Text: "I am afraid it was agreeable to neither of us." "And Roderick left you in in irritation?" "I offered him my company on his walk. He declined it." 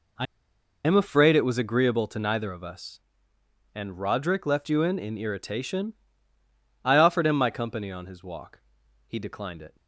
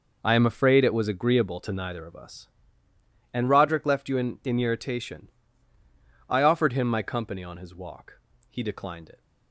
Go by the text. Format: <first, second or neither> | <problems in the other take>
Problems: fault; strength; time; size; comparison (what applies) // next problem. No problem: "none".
second | pauses between "I" and "am"; noticeable; at 0.2 s; 0.61 s long